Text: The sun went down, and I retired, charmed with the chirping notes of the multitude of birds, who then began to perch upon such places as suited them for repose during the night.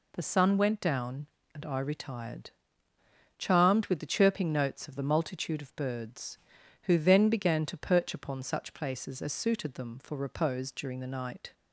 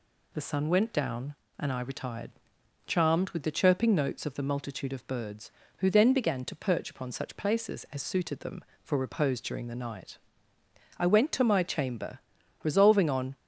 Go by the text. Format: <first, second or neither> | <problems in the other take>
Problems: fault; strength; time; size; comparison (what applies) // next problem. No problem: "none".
first | goes on to say "I went to my chamber resolving on"; strong; from 10.9 s on; 2.3 s long